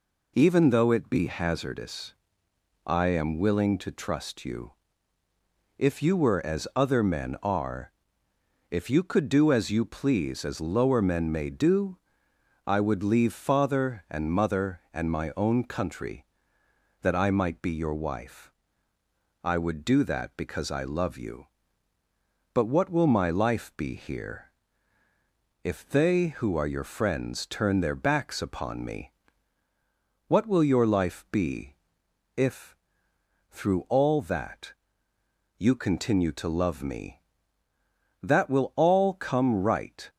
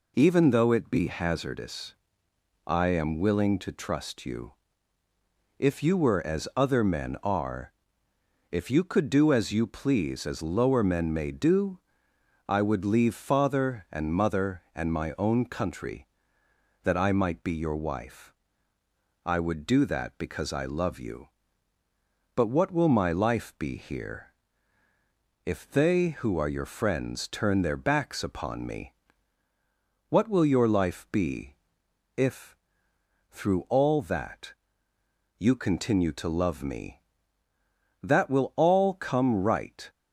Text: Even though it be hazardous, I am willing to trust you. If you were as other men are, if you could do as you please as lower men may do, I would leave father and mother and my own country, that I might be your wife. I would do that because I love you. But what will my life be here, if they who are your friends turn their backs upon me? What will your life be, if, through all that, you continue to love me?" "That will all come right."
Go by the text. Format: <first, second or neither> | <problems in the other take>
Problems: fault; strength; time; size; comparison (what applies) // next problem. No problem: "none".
neither | none